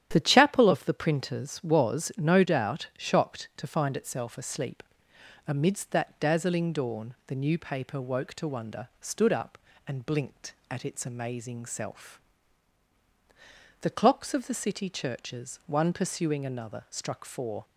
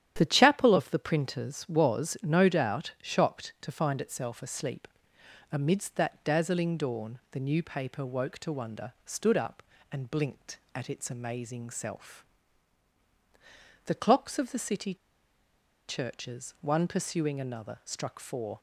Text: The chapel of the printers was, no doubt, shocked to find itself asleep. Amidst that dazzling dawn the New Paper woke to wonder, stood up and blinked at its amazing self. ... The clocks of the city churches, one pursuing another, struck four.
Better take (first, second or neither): first